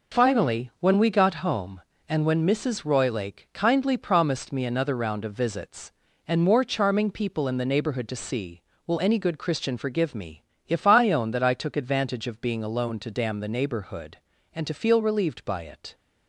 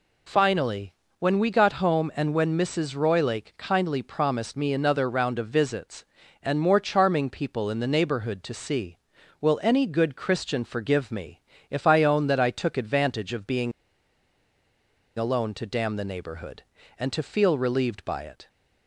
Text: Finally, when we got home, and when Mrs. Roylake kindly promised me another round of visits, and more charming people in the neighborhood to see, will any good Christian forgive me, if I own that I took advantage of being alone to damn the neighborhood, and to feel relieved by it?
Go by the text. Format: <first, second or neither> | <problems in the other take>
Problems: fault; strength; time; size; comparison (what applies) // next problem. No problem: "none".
first | pauses between "being" and "alone"; strong; at 13.7 s; 1.4 s long